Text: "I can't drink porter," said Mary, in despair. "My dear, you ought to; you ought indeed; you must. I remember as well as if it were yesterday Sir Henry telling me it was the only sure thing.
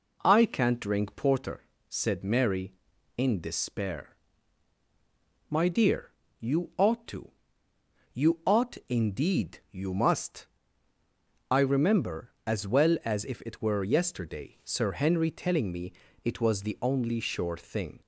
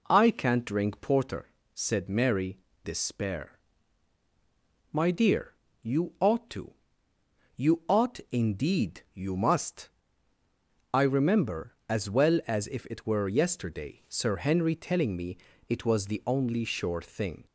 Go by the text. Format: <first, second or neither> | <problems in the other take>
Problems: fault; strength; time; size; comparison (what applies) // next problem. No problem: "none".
first | skips "in"; at 2.7 s // pauses between "me" and "it"; slight; at 15.3 s; 0.32 s long; slight in the first